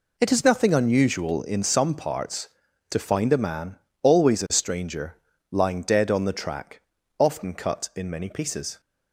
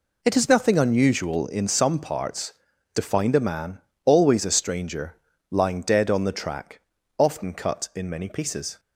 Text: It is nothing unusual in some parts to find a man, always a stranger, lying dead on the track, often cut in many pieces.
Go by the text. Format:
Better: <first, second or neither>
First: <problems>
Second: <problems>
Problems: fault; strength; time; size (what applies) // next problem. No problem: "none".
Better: neither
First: none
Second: none